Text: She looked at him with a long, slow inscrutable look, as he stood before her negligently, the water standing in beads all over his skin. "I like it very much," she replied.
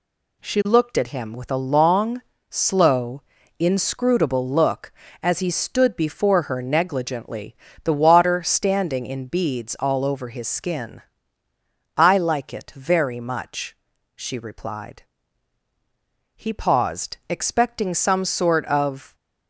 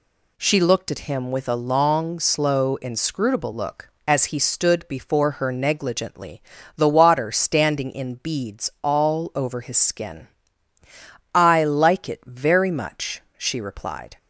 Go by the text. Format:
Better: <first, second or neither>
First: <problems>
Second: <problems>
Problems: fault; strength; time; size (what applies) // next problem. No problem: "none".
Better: second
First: pauses between "slow" and "inscrutable"; slight; at 3.2 s; 0.36 s long // goes on to say "He paused expecting some sort of"; strong; from 16.3 s on; 2.8 s long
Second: none